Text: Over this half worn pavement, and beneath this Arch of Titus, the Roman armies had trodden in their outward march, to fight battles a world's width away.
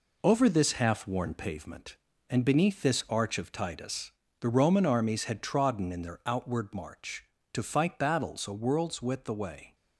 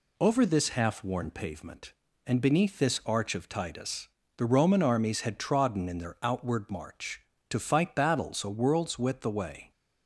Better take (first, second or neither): second